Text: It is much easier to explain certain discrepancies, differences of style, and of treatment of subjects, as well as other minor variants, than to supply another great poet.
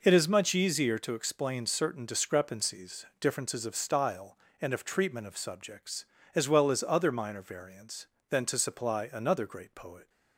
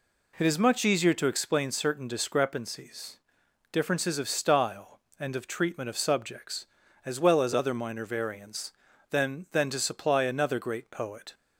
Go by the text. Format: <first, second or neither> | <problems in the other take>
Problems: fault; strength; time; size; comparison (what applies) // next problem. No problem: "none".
first | says "than" twice; at 9.5 s